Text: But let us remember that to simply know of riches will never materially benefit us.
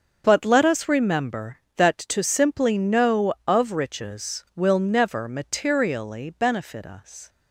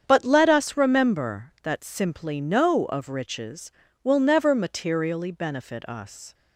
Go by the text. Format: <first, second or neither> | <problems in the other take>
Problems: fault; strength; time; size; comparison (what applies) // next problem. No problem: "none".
first | starts louder than the rest; strong; until 1.0 s; 8 dB; also in the first // skips "to"; at 1.8 s